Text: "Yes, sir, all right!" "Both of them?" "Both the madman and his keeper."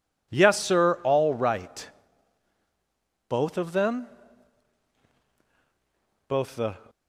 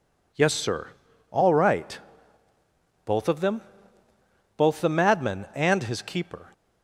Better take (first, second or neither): second